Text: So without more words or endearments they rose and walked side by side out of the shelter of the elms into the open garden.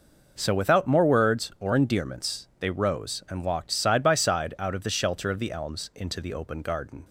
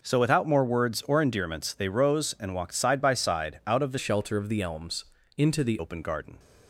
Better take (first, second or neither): first